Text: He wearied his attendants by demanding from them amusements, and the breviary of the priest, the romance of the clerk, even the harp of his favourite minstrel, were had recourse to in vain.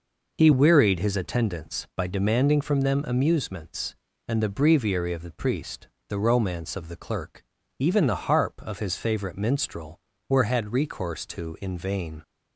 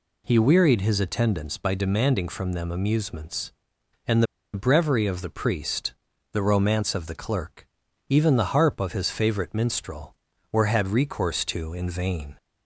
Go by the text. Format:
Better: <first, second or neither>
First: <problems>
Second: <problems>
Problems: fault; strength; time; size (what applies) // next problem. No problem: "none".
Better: first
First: none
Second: pauses between "and" and "the"; slight; at 4.2 s; 0.30 s long